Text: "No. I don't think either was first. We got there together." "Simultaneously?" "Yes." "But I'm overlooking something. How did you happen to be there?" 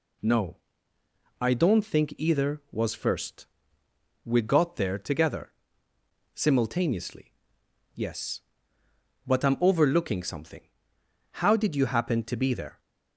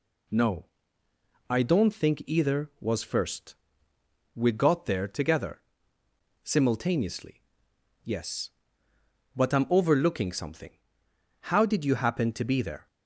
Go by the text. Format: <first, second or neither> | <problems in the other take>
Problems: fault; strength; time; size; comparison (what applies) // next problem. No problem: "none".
neither | none